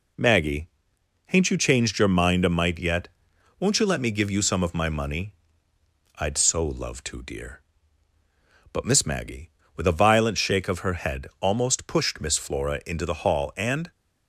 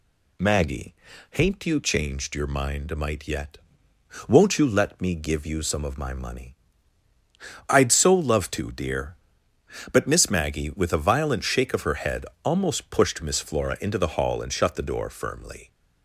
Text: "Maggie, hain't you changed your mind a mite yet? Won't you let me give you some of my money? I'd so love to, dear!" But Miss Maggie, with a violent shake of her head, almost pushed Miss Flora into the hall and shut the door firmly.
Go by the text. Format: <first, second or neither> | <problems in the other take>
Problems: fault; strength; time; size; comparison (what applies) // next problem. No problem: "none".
second | stops before "shut the door firmly"; at 13.9 s